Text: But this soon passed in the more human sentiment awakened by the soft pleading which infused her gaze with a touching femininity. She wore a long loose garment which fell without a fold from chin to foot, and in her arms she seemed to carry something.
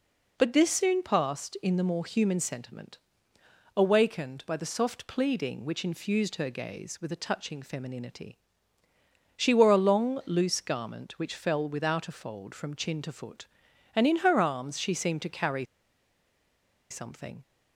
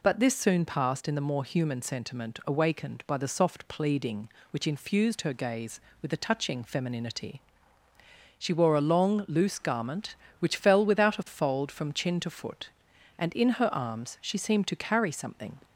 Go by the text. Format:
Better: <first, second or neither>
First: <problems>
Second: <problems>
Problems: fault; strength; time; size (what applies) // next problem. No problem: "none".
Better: second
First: pauses between "sentiment" and "awakened"; noticeable; at 2.9 s; 0.76 s long // pauses between "carry" and "something"; strong; at 15.6 s; 1.2 s long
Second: none